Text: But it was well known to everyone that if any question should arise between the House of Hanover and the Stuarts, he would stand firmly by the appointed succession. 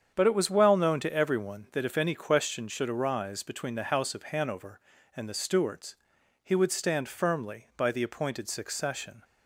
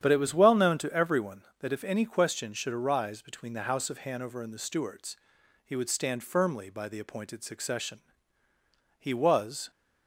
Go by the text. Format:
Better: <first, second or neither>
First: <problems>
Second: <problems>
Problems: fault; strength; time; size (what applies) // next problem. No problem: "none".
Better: first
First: starts louder than the rest; strong; until 1.1 s; 7.5 dB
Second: starts louder than the rest; strong; until 1.0 s; 9 dB // goes on to say "He was"; noticeable; from 8.9 s on; 0.72 s long